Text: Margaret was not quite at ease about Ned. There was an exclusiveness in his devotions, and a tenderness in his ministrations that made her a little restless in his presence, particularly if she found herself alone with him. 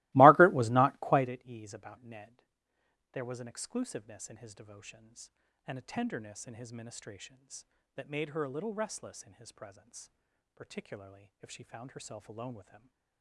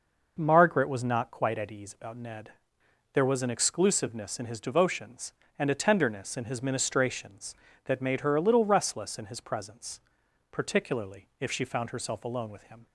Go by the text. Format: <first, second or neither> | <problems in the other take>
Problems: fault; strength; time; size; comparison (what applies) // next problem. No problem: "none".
second | starts louder than the rest; strong; until 1.3 s; 21.5 dB